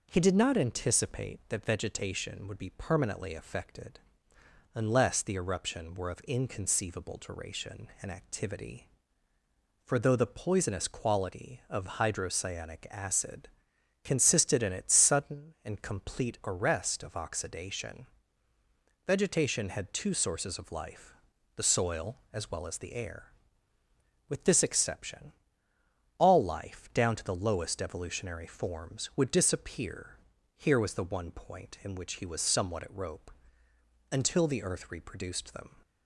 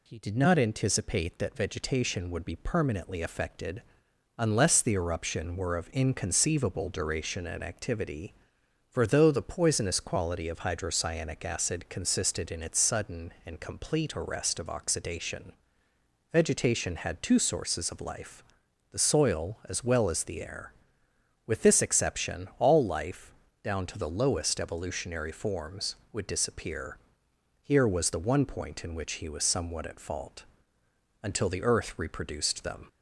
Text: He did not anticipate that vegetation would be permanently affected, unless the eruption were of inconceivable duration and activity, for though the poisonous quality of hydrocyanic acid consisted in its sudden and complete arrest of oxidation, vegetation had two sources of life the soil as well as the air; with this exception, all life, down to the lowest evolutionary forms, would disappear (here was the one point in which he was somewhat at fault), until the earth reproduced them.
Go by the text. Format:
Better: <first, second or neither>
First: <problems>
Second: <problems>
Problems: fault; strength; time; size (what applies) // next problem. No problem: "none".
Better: second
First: pauses between "acid" and "consisted"; noticeable; at 13.4 s; 0.54 s long // pauses between "life" and "the"; at 21.1 s; 0.42 s long // says "rope" for "fault"; at 32.9 s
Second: pauses between "life" and "the"; noticeable; at 18.4 s; 0.48 s long